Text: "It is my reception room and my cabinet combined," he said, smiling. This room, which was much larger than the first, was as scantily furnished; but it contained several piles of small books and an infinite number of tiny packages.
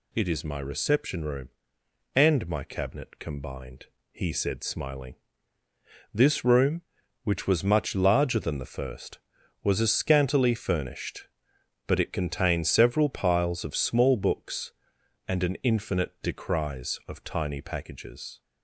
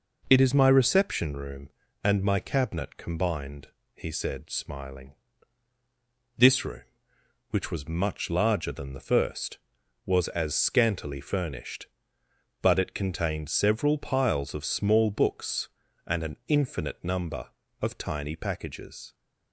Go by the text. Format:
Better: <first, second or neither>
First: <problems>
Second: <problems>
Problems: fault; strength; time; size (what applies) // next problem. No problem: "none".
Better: second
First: says "decries" for "number"; at 16.2 s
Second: none